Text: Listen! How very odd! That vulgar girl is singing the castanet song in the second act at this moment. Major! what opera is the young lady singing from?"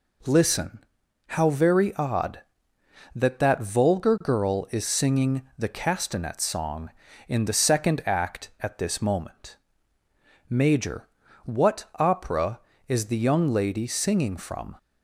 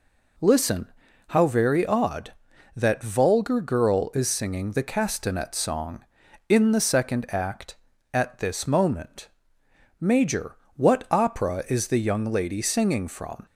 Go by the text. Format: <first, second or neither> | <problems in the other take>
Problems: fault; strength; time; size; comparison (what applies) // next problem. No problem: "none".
second | says "That" twice; at 3.3 s // pauses between "singing" and "the"; slight; at 5.4 s; 0.16 s long // pauses between "what" and "opera"; slight; at 11.8 s; 0.16 s long